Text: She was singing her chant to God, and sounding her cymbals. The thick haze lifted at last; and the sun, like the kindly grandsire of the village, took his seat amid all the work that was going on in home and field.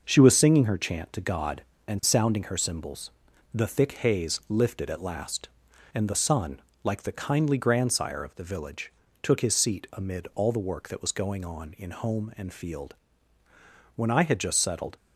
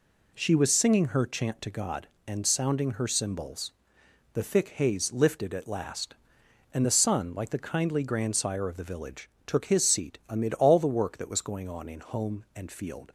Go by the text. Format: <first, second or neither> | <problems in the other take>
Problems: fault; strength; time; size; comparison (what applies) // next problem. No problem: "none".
second | goes on to say "When I had just settled"; noticeable; from 13.9 s on; 1.0 s long